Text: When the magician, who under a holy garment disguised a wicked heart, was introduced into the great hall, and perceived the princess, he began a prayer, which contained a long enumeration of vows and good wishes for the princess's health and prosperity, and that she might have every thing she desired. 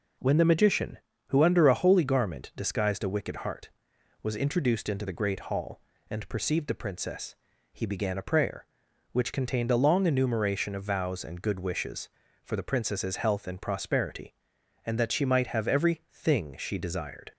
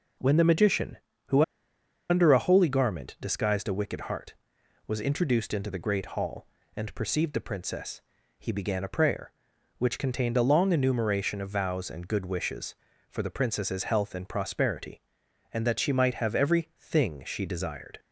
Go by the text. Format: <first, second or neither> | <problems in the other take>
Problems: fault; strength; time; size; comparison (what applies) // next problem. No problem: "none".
first | pauses between "who" and "under"; noticeable; at 1.4 s; 0.66 s long